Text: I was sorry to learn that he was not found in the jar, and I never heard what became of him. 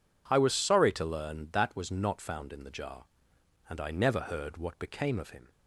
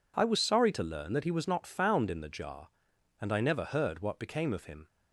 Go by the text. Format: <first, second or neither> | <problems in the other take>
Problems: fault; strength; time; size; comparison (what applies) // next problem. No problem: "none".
second | skips "he"; at 1.7 s